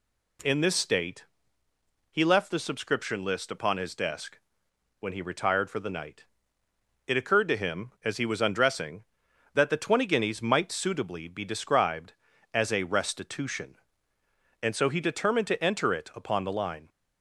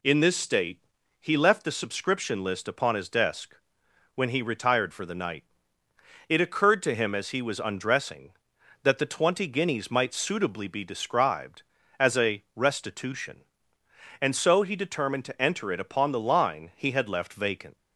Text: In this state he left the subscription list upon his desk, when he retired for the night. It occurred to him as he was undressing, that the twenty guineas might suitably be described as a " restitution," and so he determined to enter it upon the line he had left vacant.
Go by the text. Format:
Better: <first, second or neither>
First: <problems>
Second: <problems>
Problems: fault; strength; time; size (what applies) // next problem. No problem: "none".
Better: second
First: pauses between "state" and "he"; noticeable; at 1.2 s; 0.86 s long // stops before "he had left vacant"; at 16.8 s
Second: pauses between "state" and "he"; at 0.7 s; 0.42 s long